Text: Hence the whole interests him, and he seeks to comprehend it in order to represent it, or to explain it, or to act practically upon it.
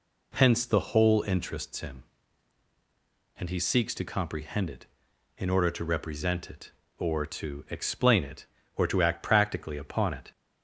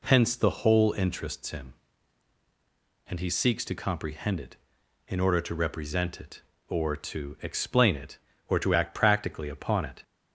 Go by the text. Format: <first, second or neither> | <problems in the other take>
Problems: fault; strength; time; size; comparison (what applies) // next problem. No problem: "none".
neither | none